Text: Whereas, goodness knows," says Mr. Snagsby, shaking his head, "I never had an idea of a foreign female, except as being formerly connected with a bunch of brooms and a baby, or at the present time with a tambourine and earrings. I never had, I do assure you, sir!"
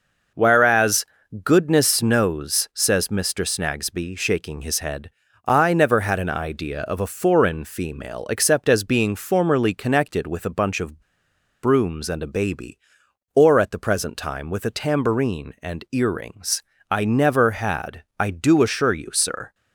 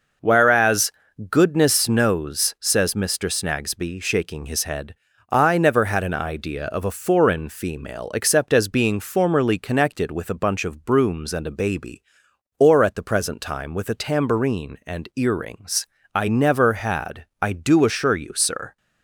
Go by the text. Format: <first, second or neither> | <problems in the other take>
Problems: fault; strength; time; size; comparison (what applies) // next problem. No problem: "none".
second | pauses between "of" and "brooms"; noticeable; at 10.9 s; 0.63 s long